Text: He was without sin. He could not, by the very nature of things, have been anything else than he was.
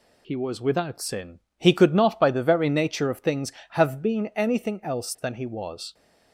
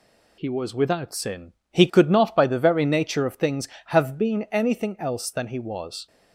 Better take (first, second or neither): neither